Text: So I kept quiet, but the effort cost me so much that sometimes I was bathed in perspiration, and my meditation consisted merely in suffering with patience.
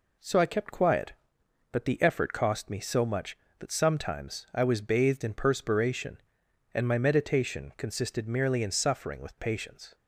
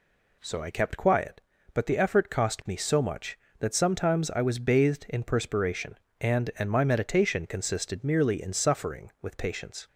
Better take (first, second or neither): first